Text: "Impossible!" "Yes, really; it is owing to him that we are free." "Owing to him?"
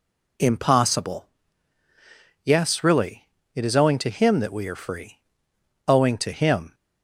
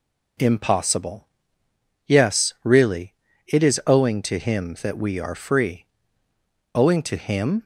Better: neither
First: none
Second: none

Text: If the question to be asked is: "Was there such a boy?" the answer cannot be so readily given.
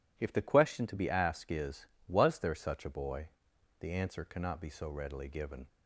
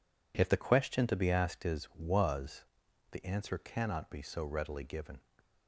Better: first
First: none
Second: skips "there such a boy"; at 2.8 s

